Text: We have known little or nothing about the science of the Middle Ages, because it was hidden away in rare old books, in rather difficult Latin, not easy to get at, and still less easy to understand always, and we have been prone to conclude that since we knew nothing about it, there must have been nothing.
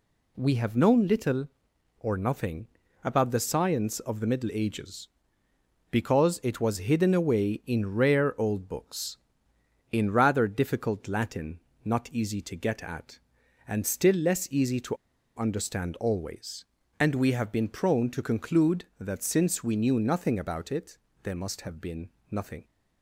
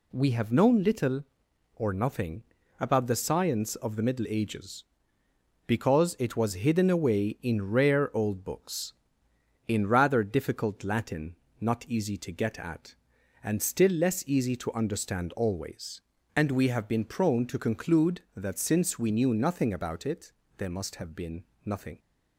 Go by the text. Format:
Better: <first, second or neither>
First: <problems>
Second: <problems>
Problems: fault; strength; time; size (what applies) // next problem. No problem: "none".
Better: second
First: pauses between "nothing" and "about"; at 2.6 s; 0.38 s long // pauses between "to" and "understand"; at 14.9 s; 0.39 s long // pauses between "been" and "nothing"; slight; at 22.0 s; 0.22 s long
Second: pauses between "nothing" and "about"; at 2.4 s; 0.38 s long // pauses between "been" and "nothing"; slight; at 21.4 s; 0.22 s long